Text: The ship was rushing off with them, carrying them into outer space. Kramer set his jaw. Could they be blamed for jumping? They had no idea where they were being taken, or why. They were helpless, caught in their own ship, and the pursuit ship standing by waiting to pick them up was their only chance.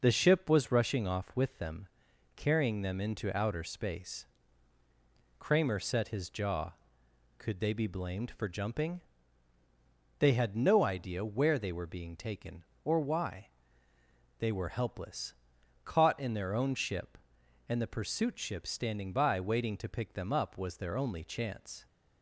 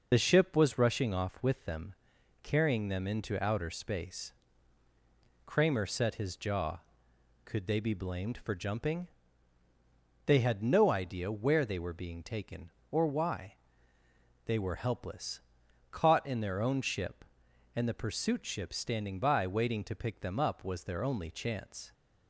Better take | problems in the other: first | loses the start of "The"; at 0.1 s; 30 ms

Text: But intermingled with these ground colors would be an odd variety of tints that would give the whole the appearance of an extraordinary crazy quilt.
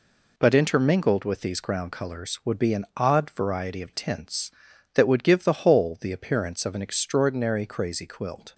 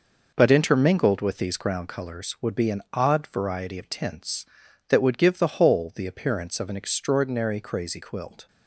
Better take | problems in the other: first | starts louder than the rest; noticeable; until 1.9 s; 5.5 dB

